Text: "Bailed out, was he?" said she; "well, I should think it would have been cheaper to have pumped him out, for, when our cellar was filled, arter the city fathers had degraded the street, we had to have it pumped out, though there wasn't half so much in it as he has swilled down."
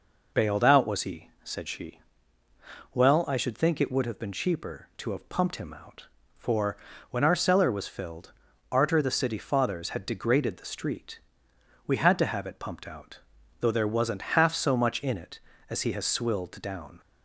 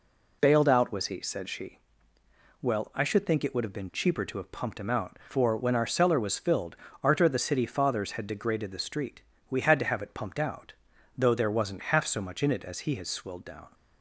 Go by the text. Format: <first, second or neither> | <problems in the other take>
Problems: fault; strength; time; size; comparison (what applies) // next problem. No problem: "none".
neither | none